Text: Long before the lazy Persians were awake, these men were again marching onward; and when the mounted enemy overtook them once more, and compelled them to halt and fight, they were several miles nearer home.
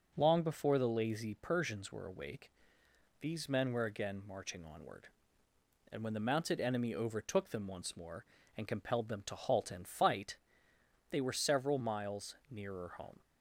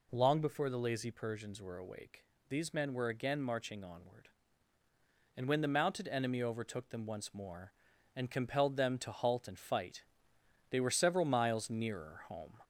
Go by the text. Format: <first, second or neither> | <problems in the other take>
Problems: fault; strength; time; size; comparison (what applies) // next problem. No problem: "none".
first | gets louder; slight; throughout; 2.5 dB